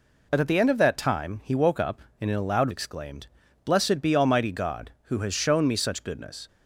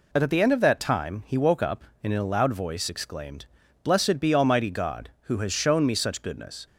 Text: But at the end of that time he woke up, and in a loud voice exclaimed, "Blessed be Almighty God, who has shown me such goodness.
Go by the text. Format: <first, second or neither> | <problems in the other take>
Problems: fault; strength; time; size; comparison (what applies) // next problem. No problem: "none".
second | skips "voice"; at 2.6 s